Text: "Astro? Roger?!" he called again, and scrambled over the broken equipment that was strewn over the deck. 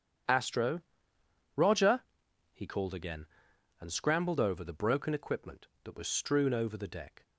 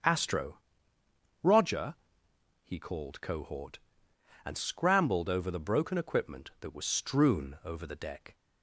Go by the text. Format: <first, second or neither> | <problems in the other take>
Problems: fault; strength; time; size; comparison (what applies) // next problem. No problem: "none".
first | starts louder than the rest; strong; until 1.8 s; 7.5 dB; strong in the first // says "cohort" for "again"; at 3.2 s